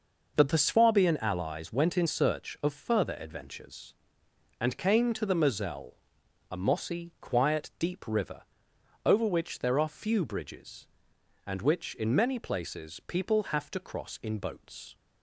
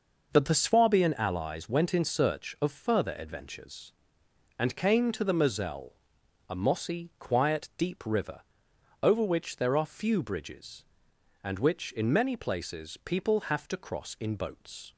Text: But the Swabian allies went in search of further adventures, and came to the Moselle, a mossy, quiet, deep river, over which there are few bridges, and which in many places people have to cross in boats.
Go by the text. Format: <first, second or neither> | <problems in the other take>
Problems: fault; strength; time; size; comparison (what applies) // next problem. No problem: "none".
neither | none